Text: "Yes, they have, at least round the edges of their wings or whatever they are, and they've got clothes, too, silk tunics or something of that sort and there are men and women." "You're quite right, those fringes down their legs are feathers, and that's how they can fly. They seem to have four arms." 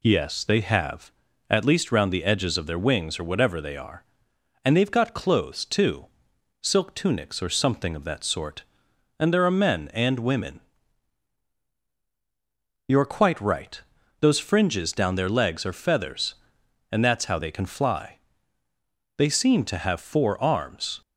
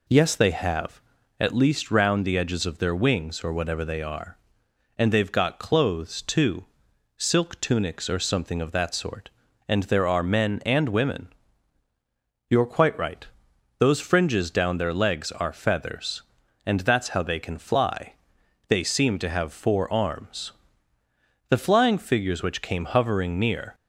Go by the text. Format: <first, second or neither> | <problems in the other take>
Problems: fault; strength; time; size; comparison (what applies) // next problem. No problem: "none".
first | goes on to say "The flying figures which came hovering near"; strong; from 21.4 s on; 2.2 s long